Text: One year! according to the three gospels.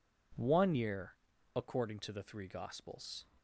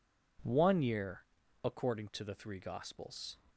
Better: neither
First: none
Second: none

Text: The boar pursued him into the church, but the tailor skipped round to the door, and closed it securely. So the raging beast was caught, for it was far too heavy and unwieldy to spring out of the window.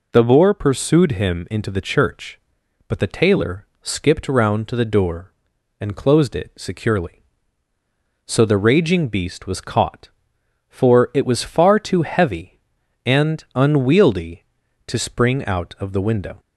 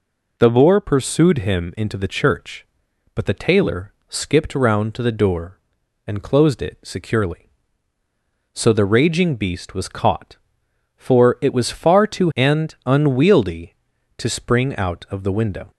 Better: first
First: pauses between "tailor" and "skipped"; slight; at 3.6 s; 0.16 s long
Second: pauses between "tailor" and "skipped"; slight; at 3.9 s; 0.16 s long // skips "heavy"; at 12.3 s

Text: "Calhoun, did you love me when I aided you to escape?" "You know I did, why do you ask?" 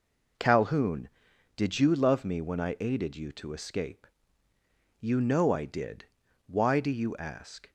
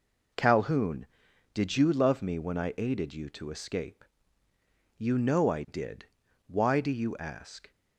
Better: neither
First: none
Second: none

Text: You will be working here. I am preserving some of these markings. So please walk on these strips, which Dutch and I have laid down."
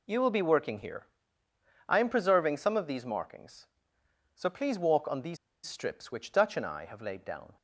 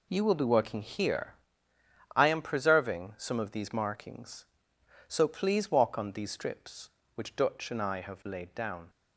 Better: second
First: pauses between "these" and "strips"; slight; at 5.3 s; 0.29 s long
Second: none

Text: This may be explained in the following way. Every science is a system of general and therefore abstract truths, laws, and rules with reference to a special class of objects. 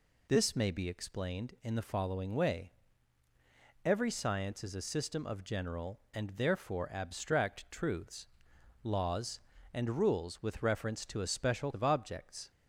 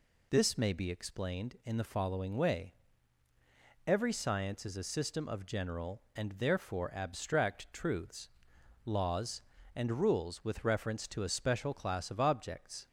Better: second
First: skips "class"; at 11.7 s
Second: none

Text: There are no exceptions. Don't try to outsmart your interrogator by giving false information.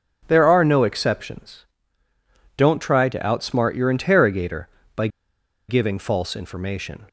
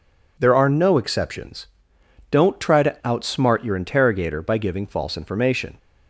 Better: second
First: starts louder than the rest; strong; until 1.2 s; 7.5 dB // pauses between "by" and "giving"; noticeable; at 5.0 s; 0.60 s long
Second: none

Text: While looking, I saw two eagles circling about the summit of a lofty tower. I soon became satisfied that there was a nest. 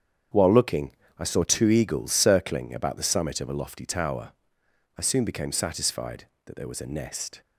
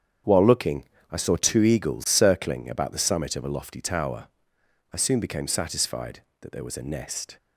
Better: neither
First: starts louder than the rest; strong; until 1.6 s; 8 dB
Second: starts louder than the rest; strong; until 1.5 s; 8 dB

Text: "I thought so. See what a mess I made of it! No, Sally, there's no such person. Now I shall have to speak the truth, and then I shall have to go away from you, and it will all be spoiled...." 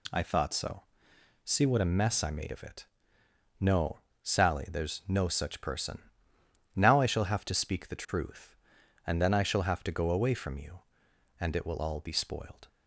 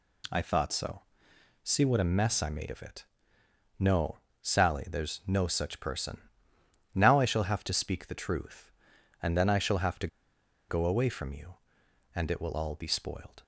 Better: first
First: none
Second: pauses between "to" and "go"; noticeable; at 10.0 s; 0.61 s long

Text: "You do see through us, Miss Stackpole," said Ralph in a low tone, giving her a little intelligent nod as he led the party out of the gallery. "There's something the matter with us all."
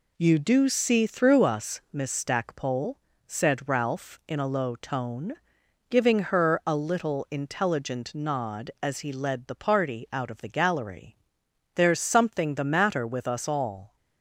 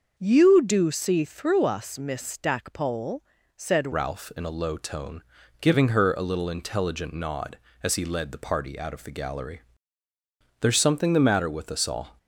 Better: first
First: none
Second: starts louder than the rest; until 1.1 s; 6 dB // changes voice at "Ralph"; from 3.9 s on; 8.2 s long

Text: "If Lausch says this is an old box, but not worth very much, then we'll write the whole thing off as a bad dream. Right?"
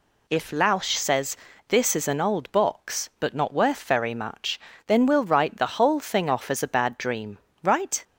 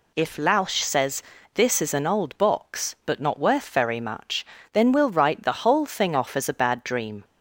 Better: first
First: pauses between "says" and "this"; slight; at 1.3 s; 0.32 s long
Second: pauses between "says" and "this"; slight; at 1.2 s; 0.32 s long // stops before "Right"; at 7.2 s

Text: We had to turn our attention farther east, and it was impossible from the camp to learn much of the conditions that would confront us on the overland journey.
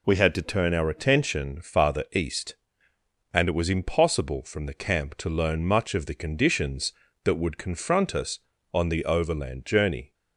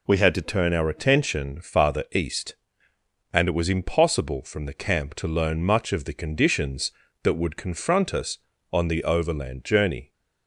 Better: neither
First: none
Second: none

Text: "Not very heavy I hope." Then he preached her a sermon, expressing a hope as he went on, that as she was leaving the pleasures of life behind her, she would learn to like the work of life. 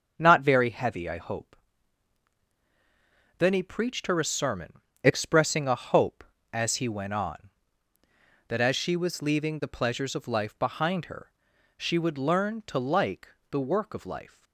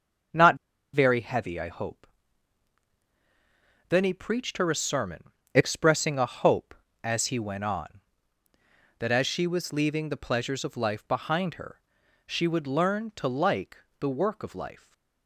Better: first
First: starts louder than the rest; until 1.1 s; 6.5 dB // pauses between "like" and "the"; slight; at 13.2 s; 0.24 s long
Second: starts louder than the rest; until 1.7 s; 6.5 dB // pauses between "Not" and "very"; at 0.5 s; 0.38 s long // pauses between "like" and "the"; slight; at 13.7 s; 0.24 s long // stays silent after the last word; slight; from 14.7 s on; 0.5 s long

